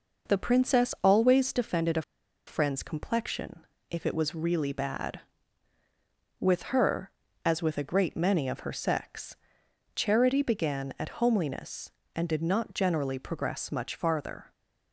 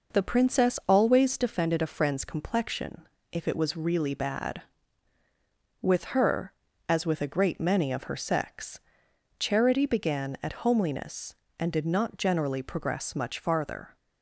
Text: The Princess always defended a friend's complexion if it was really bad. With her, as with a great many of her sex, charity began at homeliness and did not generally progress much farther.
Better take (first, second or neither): second